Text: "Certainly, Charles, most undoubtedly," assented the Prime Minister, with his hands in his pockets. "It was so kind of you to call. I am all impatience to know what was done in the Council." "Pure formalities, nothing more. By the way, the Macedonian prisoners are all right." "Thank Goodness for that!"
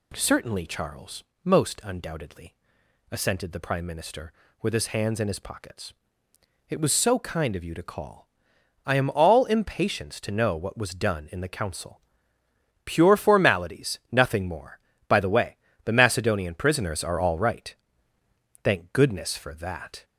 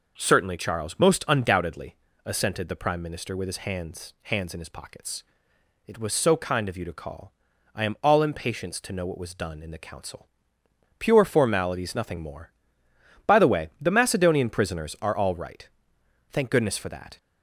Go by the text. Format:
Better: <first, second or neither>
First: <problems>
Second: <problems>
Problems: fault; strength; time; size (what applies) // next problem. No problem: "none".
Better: first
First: none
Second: says "hands" twice; at 4.2 s